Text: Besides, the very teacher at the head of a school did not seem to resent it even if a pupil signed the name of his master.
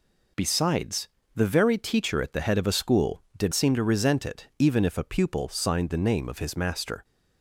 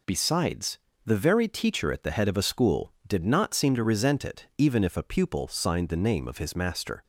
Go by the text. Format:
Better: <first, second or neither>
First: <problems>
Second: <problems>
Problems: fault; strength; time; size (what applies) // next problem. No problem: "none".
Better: second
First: skips "not"; at 3.5 s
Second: none